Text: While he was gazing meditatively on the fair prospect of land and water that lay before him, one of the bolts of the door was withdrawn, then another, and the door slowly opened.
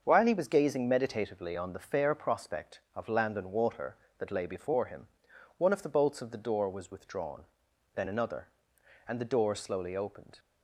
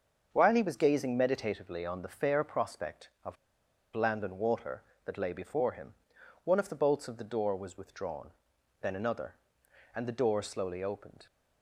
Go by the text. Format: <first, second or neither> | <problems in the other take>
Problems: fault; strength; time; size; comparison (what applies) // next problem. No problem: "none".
first | starts louder than the rest; until 1.3 s; 6.5 dB; also in the first // pauses between "of" and "land"; noticeable; at 3.3 s; 0.60 s long